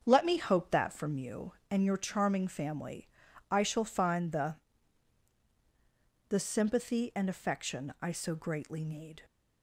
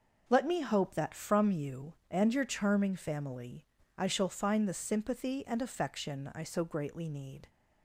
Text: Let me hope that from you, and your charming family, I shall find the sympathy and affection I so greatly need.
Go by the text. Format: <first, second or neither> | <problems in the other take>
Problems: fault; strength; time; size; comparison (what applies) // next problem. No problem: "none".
second | starts louder than the rest; strong; until 1.0 s; 7.5 dB // says "the" twice; at 6.2 s